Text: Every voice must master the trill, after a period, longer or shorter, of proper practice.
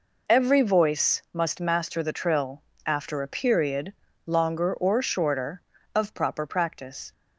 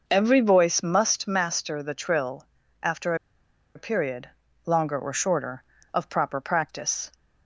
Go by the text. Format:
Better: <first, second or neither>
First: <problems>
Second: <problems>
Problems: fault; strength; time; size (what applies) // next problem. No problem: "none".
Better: first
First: none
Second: pauses between "after" and "a"; noticeable; at 3.1 s; 0.59 s long